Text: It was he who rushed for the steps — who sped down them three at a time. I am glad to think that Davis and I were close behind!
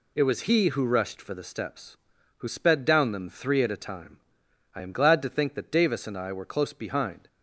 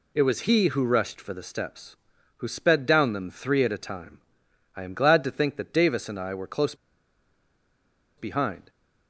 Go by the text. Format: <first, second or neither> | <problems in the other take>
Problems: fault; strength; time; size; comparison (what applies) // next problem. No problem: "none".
first | pauses between "close" and "behind"; strong; at 6.7 s; 1.4 s long